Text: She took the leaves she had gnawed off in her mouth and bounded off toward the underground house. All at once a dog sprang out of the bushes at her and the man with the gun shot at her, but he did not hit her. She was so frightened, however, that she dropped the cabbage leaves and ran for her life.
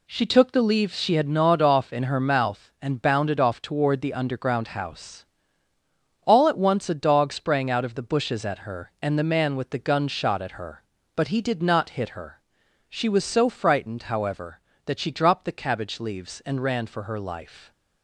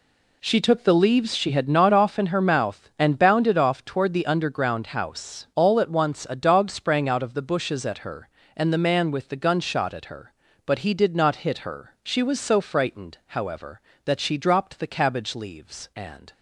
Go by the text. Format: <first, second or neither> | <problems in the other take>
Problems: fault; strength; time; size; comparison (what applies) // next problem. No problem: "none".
first | stops before "ran for her life"; at 16.3 s